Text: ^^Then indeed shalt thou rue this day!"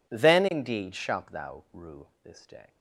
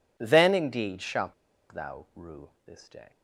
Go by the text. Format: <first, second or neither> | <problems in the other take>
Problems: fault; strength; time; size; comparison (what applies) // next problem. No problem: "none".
first | pauses between "shalt" and "thou"; at 1.3 s; 0.38 s long // pauses between "rue" and "this"; slight; at 2.4 s; 0.18 s long; slight in the first